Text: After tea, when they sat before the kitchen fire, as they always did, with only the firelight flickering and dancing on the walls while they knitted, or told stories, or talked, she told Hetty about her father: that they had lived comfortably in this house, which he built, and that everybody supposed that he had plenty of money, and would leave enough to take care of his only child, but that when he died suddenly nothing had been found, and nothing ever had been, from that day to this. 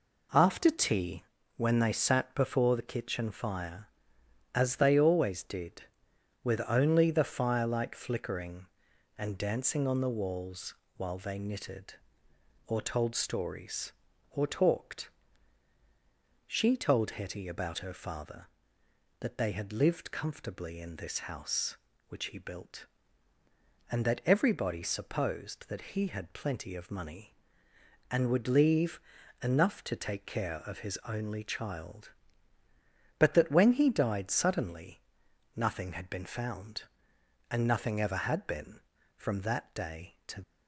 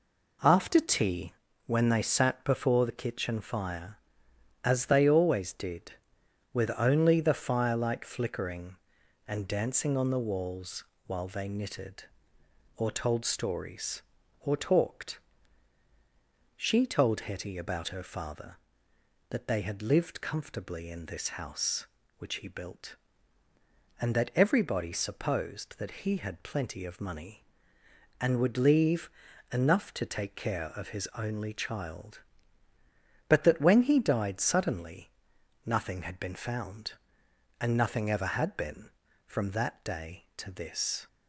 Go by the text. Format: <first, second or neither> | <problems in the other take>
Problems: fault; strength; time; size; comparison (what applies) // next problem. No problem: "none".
second | pauses between "walls" and "while"; slight; at 10.7 s; 0.22 s long; slight in the second // pauses between "leave" and "enough"; at 28.9 s; 0.42 s long; also in the second // pauses between "suddenly" and "nothing"; noticeable; at 34.9 s; 0.56 s long; noticeable in the second // stops before "this"; at 40.4 s